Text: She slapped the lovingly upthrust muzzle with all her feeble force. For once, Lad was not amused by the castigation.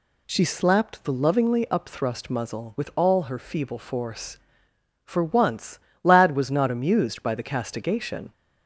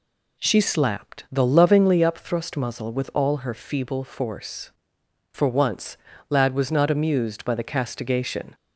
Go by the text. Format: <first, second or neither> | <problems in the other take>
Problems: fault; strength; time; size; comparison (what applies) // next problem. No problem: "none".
neither | none